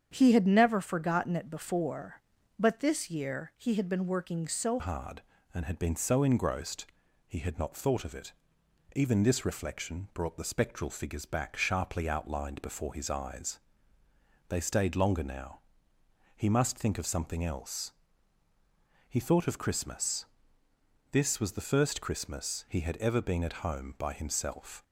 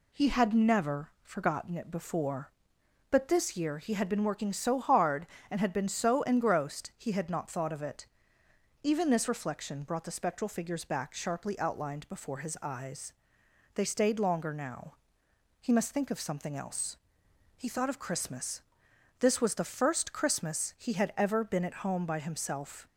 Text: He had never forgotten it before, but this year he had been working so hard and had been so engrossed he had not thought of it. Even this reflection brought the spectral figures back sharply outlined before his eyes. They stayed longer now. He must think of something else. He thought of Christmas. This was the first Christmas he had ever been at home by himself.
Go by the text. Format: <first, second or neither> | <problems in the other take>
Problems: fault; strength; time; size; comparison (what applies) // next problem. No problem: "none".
second | starts louder than the rest; strong; until 1.1 s; 8 dB // changes voice at "hard"; from 4.7 s on; 20.1 s long // pauses between "engrossed" and "he"; at 6.8 s; 0.42 s long